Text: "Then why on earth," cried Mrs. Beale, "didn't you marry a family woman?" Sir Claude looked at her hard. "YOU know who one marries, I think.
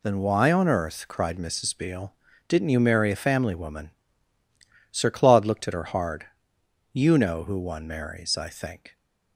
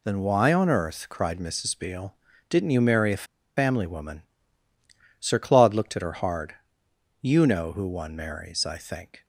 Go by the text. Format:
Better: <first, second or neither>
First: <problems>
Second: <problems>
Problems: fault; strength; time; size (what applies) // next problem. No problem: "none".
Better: first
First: none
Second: pauses between "a" and "family"; slight; at 3.2 s; 0.30 s long